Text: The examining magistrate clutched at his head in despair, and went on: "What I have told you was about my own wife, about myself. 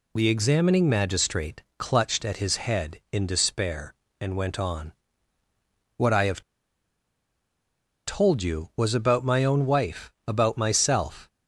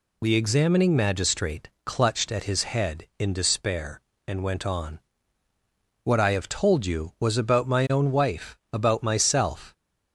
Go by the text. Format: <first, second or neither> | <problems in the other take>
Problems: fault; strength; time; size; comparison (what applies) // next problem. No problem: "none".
second | pauses between "magistrate" and "clutched"; slight; at 1.6 s; 0.16 s long; slight in the second // pauses between "have" and "told"; strong; at 6.4 s; 1.6 s long